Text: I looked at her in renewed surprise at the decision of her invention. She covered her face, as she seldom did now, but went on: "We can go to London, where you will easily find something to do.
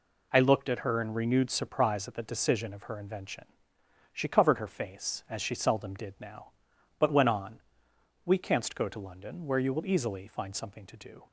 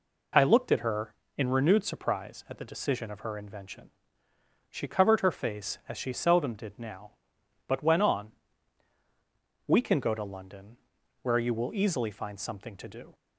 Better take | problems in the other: second | says "canst" for "can"; at 8.3 s

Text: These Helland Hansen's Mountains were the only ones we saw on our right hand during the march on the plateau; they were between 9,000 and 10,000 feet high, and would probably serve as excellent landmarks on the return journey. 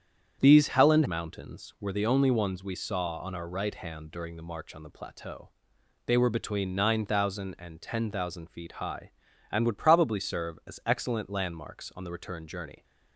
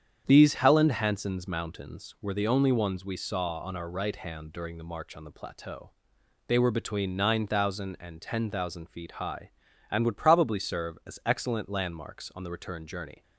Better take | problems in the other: second | starts louder than the rest; strong; until 1.4 s; 8.5 dB; strong in the second // skips "Hansen's"; at 1.0 s

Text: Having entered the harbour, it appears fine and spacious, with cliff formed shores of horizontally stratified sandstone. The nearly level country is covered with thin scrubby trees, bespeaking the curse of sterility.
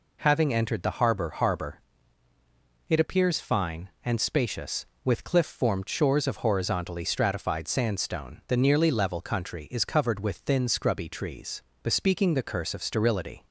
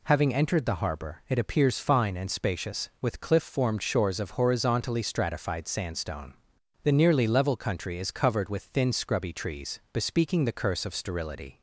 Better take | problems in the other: second | says "harbour" twice; at 1.2 s

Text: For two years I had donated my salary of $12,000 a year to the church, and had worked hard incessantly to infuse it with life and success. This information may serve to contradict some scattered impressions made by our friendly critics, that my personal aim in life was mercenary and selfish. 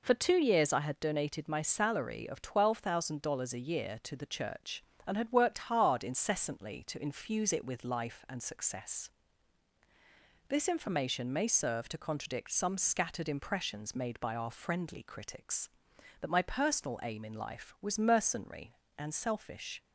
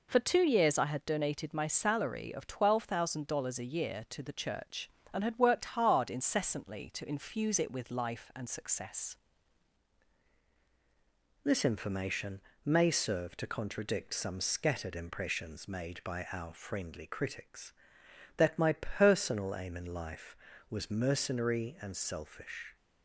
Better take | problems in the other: first | changes voice at "This"; from 11.4 s on; 11.3 s long // pauses between "information" and "may"; slight; at 12.4 s; 0.22 s long

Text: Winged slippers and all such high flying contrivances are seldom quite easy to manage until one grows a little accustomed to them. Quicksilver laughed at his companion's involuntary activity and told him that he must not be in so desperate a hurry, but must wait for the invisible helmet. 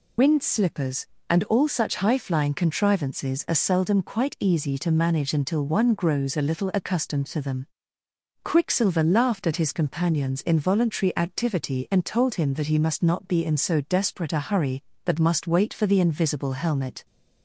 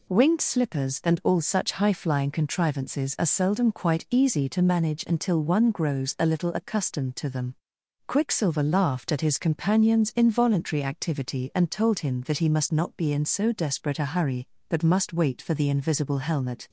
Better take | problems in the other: second | loses the start of "Winged"; at 0.1 s; 75 ms

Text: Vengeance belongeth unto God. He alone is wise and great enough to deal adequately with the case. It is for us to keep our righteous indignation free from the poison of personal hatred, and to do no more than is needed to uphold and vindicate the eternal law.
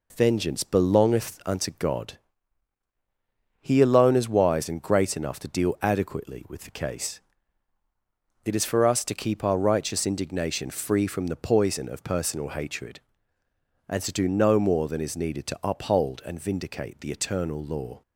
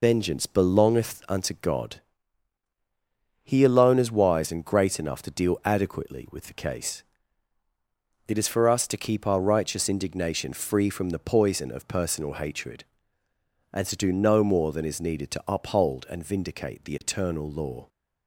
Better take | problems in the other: first | loses the start of "Vengeance"; at 0.0 s; 95 ms

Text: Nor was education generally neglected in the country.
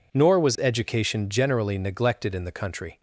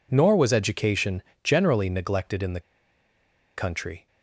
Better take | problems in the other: first | pauses between "education" and "generally"; slight; at 1.2 s; 0.22 s long // pauses between "the" and "country"; noticeable; at 2.5 s; 0.96 s long

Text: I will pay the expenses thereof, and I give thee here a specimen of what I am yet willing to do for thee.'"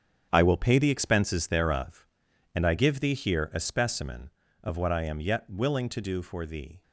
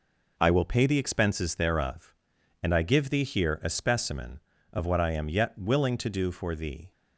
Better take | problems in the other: second | gets quieter; strong; throughout; 11 dB

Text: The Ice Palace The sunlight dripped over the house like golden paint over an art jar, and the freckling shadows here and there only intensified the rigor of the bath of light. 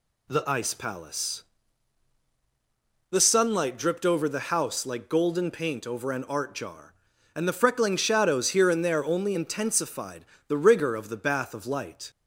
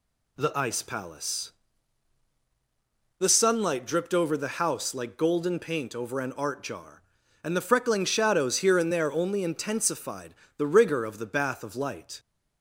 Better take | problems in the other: neither | pauses between "Palace" and "The"; strong; the same in both // pauses between "intensified" and "the"; slight; the same in both

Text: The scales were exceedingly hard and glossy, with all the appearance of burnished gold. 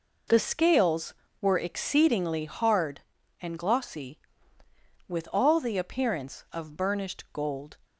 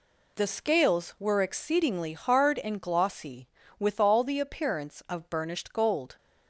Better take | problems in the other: neither | none

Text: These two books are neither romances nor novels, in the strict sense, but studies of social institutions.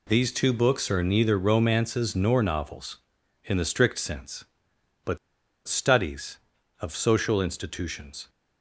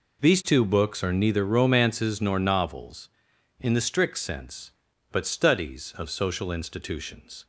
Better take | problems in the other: second | pauses between "but" and "studies"; noticeable; at 5.1 s; 0.49 s long

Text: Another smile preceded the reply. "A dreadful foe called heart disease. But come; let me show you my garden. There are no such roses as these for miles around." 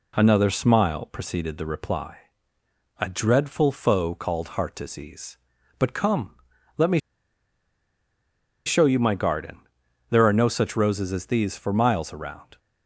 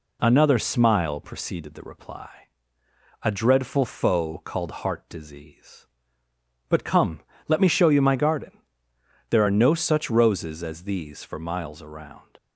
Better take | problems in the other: second | pauses between "me" and "show"; strong; at 7.0 s; 1.6 s long

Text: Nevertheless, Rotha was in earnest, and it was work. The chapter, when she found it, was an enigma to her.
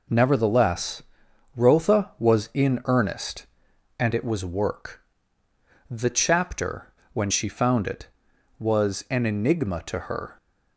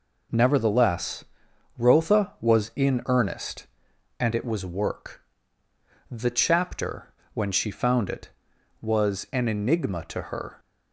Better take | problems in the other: neither | none

